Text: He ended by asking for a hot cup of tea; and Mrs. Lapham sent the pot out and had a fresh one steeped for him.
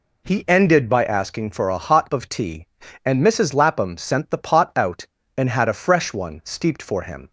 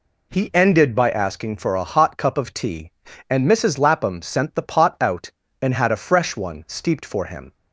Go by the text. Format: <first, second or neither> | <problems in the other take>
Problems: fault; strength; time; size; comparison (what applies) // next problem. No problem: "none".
second | skips "cup"; at 2.1 s